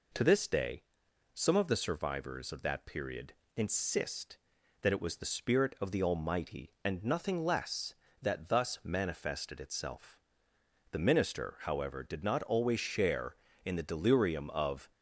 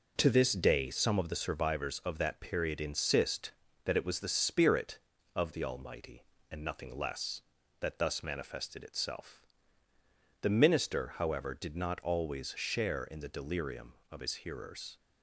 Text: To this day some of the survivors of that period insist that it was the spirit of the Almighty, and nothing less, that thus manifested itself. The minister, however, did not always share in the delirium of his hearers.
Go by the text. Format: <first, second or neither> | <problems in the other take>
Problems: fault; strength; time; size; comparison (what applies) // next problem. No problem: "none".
second | pauses between "day" and "some"; noticeable; at 0.8 s; 0.50 s long // pauses between "period" and "insist"; slight; at 3.3 s; 0.24 s long // stops before "his hearers"; at 14.9 s